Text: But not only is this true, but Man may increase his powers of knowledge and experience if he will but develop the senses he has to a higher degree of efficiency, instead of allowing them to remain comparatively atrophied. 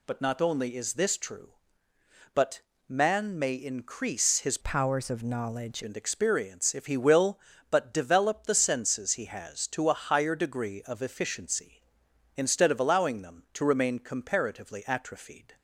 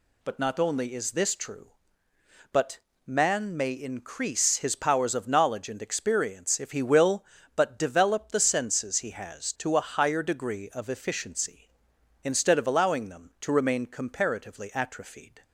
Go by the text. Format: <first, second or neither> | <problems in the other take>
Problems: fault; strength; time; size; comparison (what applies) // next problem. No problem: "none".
second | pauses between "but" and "Man"; slight; at 2.6 s; 0.28 s long; slight in the second // changes voice from "powers" to "knowledge"; from 4.6 to 5.8 s; 1.2 s long